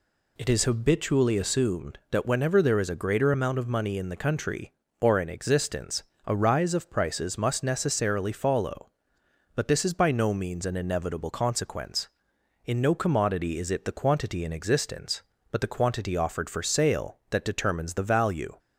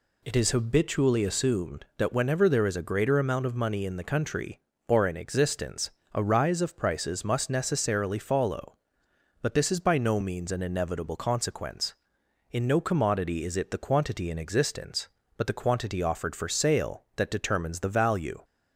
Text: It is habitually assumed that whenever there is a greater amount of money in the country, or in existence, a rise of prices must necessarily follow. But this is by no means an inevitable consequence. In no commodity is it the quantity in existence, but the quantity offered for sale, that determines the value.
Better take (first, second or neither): neither